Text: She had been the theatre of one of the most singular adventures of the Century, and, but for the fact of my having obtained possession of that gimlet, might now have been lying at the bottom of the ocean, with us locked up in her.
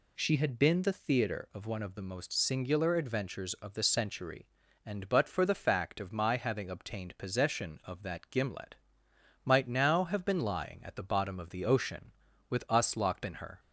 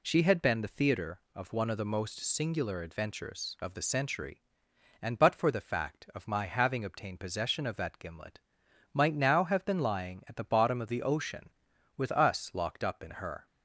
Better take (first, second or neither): second